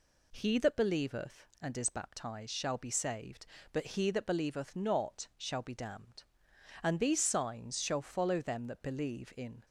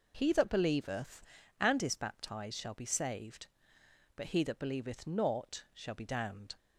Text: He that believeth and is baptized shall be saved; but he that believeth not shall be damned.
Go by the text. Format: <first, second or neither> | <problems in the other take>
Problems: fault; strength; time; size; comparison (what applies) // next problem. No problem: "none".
second | goes on to say "And these signs shall follow them that believe in"; strong; from 6.8 s on; 2.8 s long